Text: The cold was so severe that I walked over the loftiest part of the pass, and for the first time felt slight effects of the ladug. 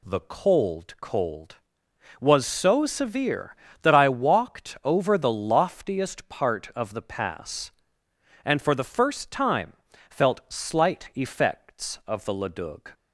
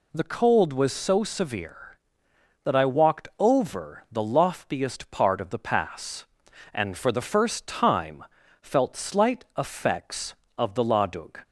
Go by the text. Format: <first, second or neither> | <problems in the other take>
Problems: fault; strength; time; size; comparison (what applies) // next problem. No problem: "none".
second | says "cold" twice; at 0.9 s // pauses between "time" and "felt"; slight; at 9.7 s; 0.36 s long; slight in the second